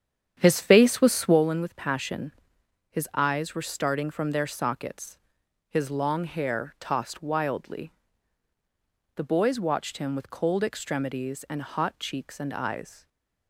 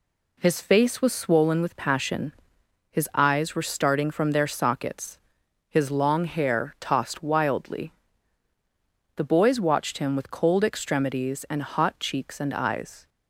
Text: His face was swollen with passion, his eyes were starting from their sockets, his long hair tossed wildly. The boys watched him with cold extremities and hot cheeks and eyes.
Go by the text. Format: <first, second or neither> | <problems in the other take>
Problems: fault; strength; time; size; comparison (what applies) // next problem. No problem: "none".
second | starts louder than the rest; strong; until 1.5 s; 9 dB // stays silent after the last word; slight; from 12.9 s on; 0.5 s long